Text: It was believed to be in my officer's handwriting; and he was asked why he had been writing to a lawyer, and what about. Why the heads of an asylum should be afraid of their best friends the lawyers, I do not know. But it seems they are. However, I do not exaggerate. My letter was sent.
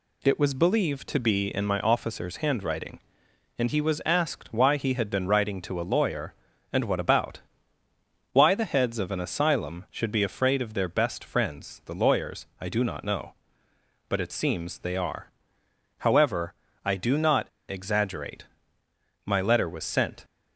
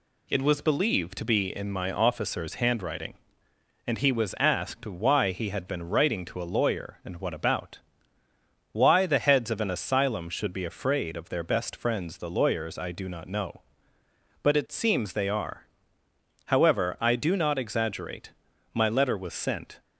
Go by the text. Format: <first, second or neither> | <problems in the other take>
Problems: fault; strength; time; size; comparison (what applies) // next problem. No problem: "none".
second | pauses between "not" and "exaggerate"; slight; at 17.4 s; 0.20 s long